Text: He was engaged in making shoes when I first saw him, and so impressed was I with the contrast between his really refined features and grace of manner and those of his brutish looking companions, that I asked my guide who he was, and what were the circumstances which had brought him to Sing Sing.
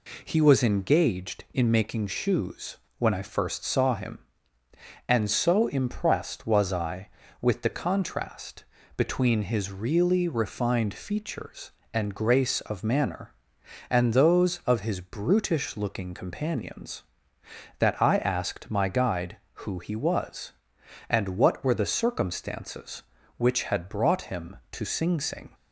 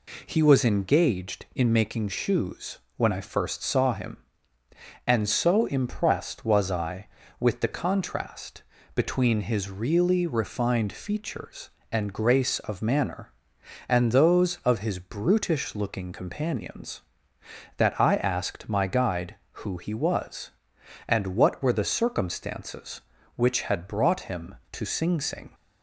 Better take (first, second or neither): neither